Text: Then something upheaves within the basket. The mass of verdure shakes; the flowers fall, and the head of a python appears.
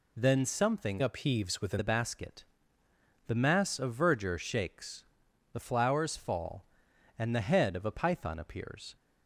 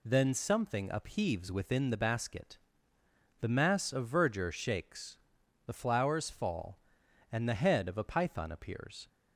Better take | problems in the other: second | changes voice from "upheaves" to "within"; from 1.0 to 1.7 s; 0.7 s long

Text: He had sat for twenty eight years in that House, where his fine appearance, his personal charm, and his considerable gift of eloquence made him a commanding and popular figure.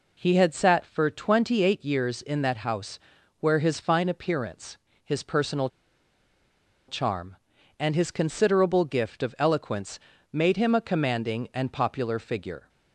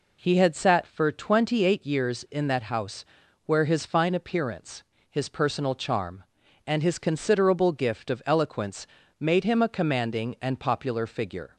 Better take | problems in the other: second | pauses between "personal" and "charm"; at 5.6 s; 1.2 s long // pauses between "eloquence" and "made"; slight; at 9.9 s; 0.34 s long; slight in the second

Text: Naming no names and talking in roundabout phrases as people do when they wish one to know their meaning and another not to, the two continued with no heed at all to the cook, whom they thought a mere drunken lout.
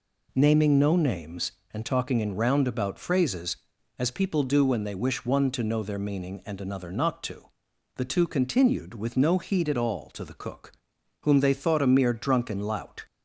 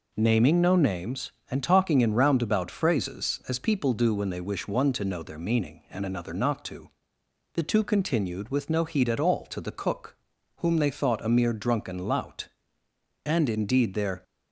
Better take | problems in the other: first | goes on to say "And indeed their"; noticeable; from 13.2 s on; 0.98 s long

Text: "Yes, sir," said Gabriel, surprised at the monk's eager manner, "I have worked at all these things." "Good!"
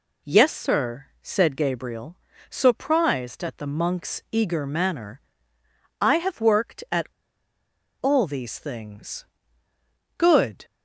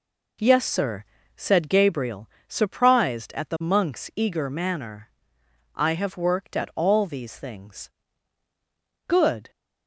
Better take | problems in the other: second | pauses between "at" and "all"; noticeable; at 7.0 s; 0.93 s long

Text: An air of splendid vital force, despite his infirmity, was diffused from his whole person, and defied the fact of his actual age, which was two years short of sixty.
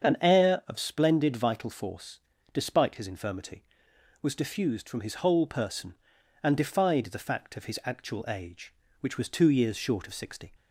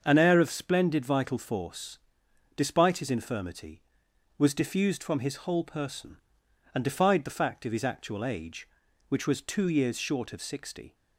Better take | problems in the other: neither | starts louder than the rest; the same in both

